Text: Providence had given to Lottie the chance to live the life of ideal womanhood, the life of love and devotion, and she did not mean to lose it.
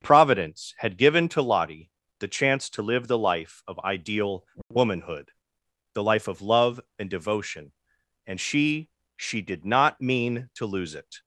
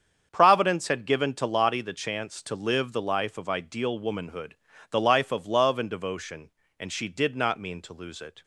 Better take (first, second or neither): second